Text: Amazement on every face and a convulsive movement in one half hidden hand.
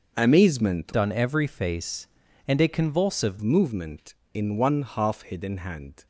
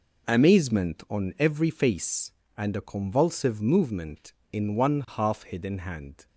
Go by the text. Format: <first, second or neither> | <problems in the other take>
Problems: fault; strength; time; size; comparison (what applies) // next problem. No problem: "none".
second | starts louder than the rest; until 1.2 s; 6 dB // changes voice from "on" to "convulsive"; from 0.9 to 3.3 s; 2.4 s long